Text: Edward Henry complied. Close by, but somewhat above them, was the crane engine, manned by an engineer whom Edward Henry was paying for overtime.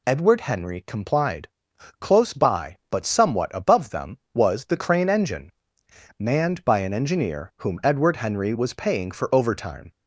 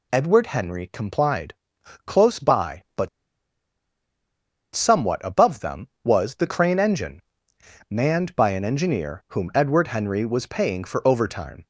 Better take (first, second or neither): first